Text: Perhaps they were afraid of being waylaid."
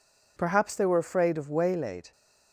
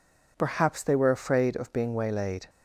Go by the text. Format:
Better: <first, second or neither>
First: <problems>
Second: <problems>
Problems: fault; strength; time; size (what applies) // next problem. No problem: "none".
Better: second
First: skips "being"; at 1.4 s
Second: none